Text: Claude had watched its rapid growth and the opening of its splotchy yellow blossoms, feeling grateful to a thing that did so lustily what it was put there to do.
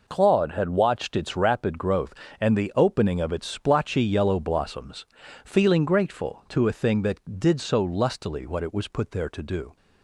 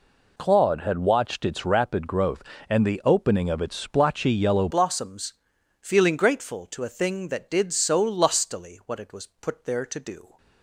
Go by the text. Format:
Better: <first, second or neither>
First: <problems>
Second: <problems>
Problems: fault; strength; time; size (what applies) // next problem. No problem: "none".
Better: first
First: none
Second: changes voice at "blossoms"; from 4.6 s on; 5.7 s long